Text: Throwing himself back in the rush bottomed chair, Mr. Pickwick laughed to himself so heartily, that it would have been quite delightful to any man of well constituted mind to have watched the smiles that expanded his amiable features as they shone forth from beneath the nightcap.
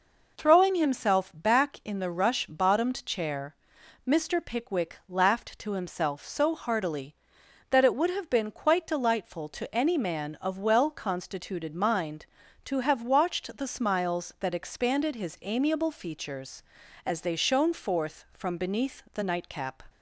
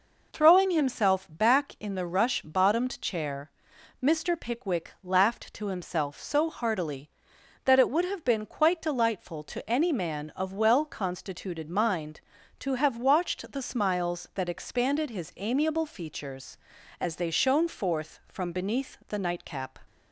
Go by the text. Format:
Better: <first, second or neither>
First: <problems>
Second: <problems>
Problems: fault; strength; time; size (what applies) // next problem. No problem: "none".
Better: neither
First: none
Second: none